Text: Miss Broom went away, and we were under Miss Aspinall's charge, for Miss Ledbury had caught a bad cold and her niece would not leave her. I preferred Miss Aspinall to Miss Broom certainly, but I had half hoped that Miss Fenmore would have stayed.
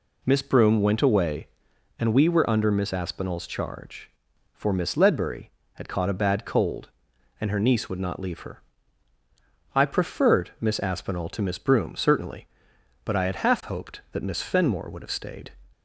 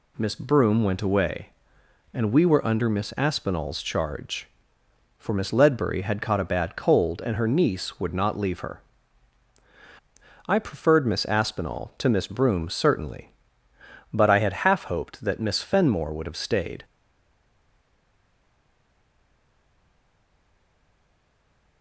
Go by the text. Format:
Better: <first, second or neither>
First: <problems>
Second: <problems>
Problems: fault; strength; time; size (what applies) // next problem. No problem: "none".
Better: first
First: none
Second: stays silent after the last word; strong; from 16.8 s on; 5.0 s long